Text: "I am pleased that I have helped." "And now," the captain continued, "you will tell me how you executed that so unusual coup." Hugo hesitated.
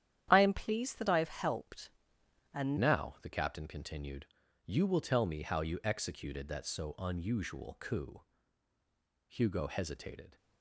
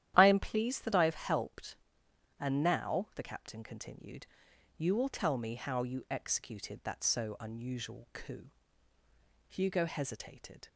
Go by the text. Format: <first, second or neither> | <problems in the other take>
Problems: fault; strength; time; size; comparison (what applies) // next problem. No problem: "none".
second | starts louder than the rest; strong; until 1.3 s; 10.5 dB; strong in the second // changes voice at "now"; from 2.7 s on; 7.6 s long